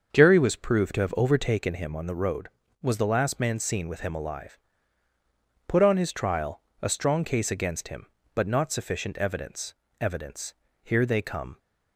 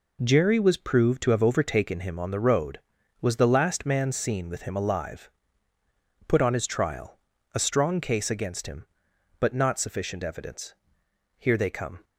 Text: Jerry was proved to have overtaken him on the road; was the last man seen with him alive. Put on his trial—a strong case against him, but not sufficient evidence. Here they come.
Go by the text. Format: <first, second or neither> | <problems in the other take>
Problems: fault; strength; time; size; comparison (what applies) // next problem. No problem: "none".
second | starts louder than the rest; until 1.1 s; 6.5 dB // says "evidence" twice; at 10.0 s